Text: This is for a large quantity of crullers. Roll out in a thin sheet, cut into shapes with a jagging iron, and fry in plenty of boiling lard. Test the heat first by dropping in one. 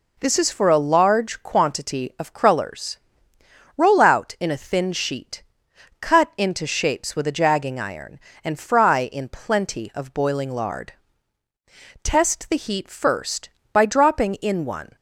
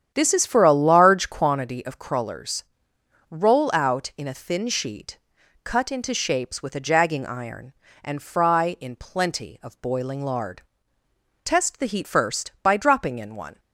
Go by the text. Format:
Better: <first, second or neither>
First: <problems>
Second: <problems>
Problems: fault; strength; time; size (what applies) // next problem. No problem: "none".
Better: first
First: none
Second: starts louder than the rest; strong; until 1.6 s; 9 dB